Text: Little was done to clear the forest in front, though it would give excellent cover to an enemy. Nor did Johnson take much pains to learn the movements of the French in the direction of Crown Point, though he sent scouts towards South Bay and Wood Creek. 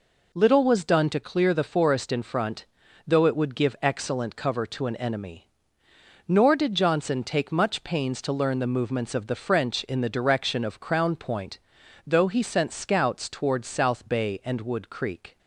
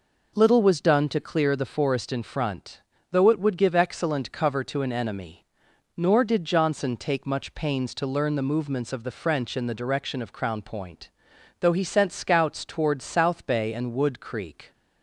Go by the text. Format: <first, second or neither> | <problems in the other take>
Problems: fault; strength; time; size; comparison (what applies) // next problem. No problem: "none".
neither | none